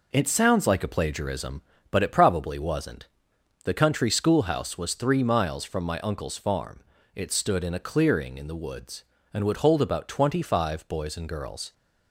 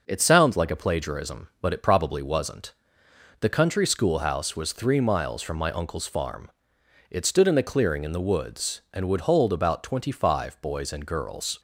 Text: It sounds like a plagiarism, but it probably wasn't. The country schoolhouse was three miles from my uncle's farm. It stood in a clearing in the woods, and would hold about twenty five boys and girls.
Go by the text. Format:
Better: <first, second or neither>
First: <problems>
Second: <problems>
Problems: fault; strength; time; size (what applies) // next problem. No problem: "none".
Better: neither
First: none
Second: none